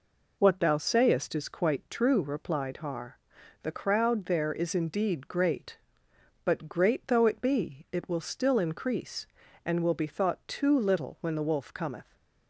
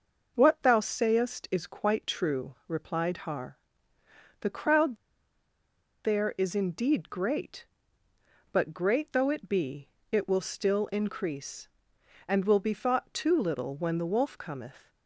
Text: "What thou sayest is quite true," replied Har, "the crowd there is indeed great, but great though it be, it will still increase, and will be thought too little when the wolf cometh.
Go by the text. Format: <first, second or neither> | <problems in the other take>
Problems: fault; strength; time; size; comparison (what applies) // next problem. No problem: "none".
first | starts louder than the rest; noticeable; until 1.3 s; 6 dB // pauses between "crowd" and "there"; at 4.9 s; 1.0 s long